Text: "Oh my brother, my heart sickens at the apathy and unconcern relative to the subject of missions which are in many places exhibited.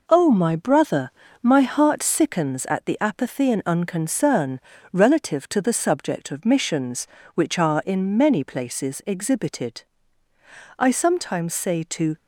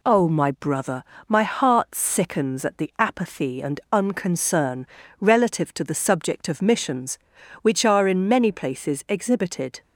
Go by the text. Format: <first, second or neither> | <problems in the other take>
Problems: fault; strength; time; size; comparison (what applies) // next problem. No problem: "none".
second | pauses between "unconcern" and "relative"; slight; at 4.6 s; 0.32 s long; slight in the second // goes on to say "I sometimes say to"; from 10.7 s on; 1.3 s long